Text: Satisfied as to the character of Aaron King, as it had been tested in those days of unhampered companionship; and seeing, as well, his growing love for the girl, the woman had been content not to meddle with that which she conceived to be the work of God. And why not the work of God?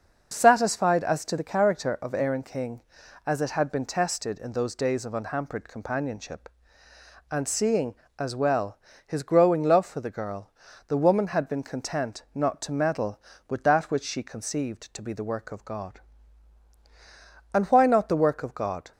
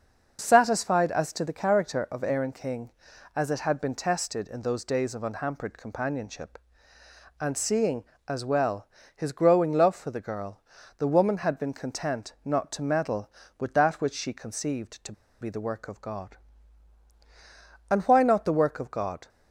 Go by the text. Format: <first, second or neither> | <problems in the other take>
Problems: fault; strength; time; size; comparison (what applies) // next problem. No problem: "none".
first | starts louder than the rest; noticeable; until 1.4 s; 6 dB; noticeable in the first // pauses between "to" and "be"; slight; at 15.1 s; 0.29 s long